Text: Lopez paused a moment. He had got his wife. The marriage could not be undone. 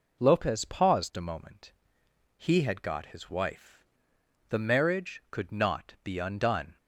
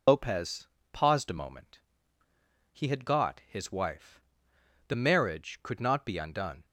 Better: first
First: none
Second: loses the start of "Lopez"; at 0.0 s; 100 ms // pauses between "Lopez" and "paused"; slight; at 0.6 s; 0.24 s long

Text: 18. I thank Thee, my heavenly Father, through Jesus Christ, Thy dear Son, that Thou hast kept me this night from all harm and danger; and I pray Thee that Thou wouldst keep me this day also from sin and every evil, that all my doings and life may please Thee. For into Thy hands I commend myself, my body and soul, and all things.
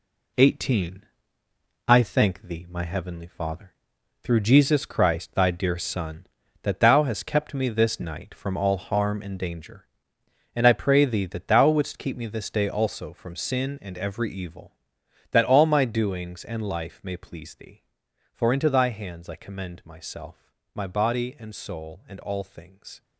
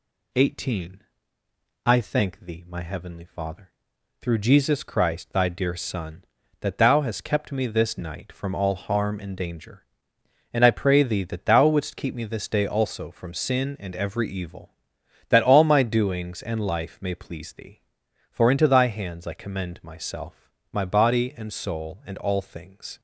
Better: second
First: gets quieter; throughout; 7 dB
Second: none

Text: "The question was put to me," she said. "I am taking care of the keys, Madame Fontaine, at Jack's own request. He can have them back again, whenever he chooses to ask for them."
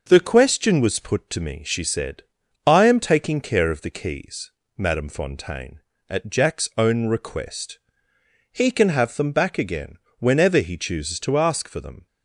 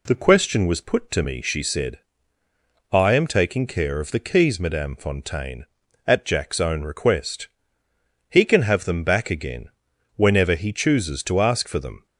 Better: neither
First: none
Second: none

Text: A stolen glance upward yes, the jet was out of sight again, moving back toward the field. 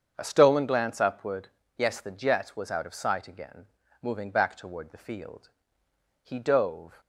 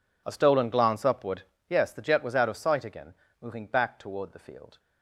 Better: second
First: starts louder than the rest; strong; until 1.1 s; 7.5 dB // pauses between "upward" and "yes"; slight; at 1.4 s; 0.28 s long // goes on to say "He dove"; noticeable; from 6.2 s on; 0.78 s long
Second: pauses between "upward" and "yes"; slight; at 1.4 s; 0.24 s long

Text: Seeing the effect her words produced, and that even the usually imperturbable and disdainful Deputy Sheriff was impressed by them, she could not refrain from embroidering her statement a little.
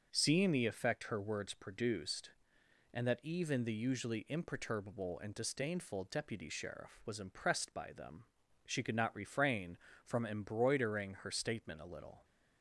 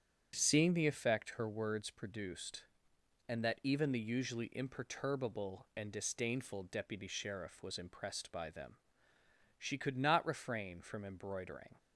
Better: first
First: starts louder than the rest; until 1.1 s; 6.5 dB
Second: starts louder than the rest; strong; until 1.3 s; 8.5 dB // stops before "her statement a little"; at 11.7 s

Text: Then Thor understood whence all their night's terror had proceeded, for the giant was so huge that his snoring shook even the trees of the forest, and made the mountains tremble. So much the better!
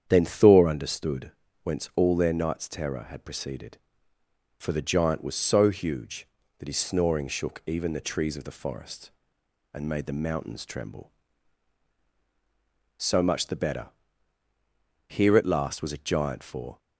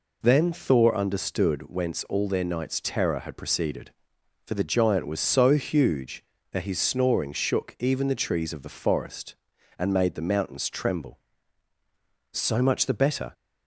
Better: second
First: starts louder than the rest; strong; until 1.0 s; 8.5 dB // pauses between "understood" and "whence"; slight; at 1.3 s; 0.32 s long // goes on to say "Here at last was a giant for"; strong; from 15.0 s on; 1.7 s long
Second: none

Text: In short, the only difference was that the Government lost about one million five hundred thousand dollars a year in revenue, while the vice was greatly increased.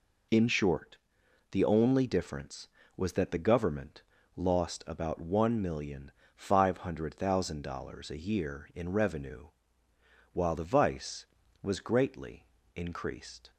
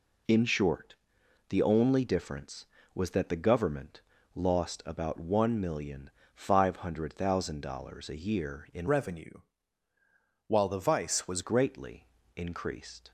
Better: first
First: pauses between "Government" and "lost"; slight; at 4.0 s; 0.32 s long // pauses between "million" and "five"; slight; at 6.1 s; 0.24 s long // pauses between "greatly" and "increased"; slight; at 12.4 s; 0.30 s long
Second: pauses between "Government" and "lost"; slight; at 4.0 s; 0.32 s long // pauses between "million" and "five"; slight; at 6.0 s; 0.24 s long // changes voice from "revenue" to "was"; from 8.8 to 11.4 s; 2.6 s long // pauses between "greatly" and "increased"; slight; at 12.0 s; 0.30 s long

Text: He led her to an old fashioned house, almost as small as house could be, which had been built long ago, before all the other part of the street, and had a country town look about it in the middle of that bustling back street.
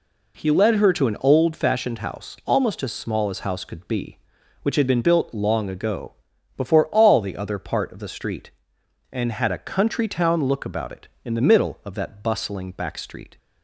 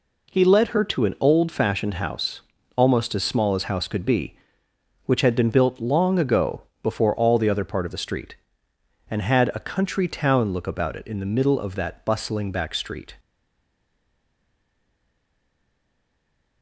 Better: first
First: none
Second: stays silent after the last word; strong; from 13.1 s on; 3.5 s long

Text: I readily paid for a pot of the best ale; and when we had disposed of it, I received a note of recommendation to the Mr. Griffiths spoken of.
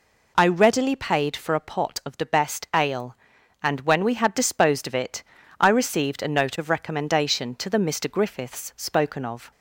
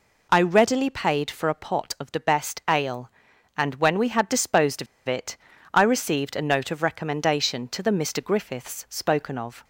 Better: first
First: none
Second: pauses between "of" and "it"; slight; at 4.8 s; 0.21 s long

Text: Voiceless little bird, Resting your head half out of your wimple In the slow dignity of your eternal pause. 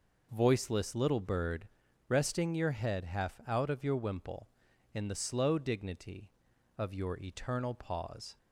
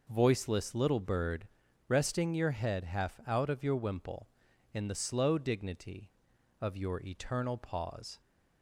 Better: neither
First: none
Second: none

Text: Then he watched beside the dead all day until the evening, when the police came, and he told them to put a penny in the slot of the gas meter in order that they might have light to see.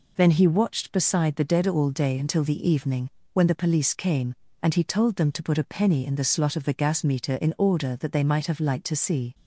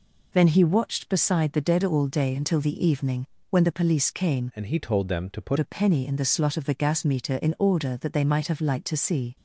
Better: first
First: none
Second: changes voice from "and" to "put"; from 4.5 to 5.5 s; 1.0 s long

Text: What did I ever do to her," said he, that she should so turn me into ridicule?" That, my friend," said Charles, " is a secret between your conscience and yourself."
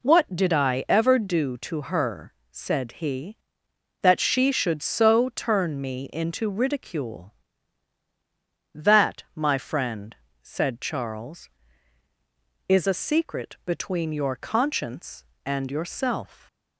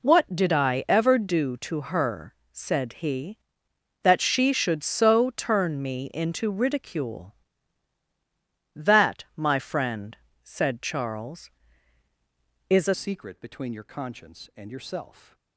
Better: first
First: none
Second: changes voice at "secret"; from 12.9 s on; 2.4 s long

